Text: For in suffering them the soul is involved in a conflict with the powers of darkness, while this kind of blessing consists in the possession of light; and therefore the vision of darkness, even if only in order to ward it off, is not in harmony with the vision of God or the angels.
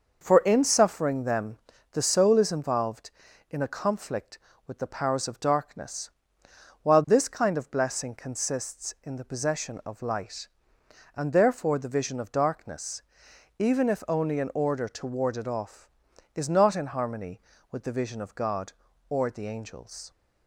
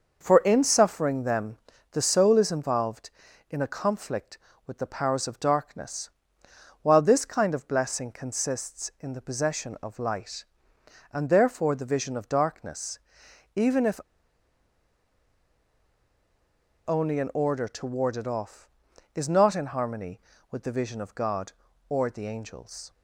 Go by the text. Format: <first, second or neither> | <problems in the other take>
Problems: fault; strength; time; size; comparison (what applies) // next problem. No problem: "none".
first | pauses between "them" and "the"; slight; at 1.5 s; 0.36 s long; slight in the first // pauses between "if" and "only"; strong; at 13.9 s; 2.8 s long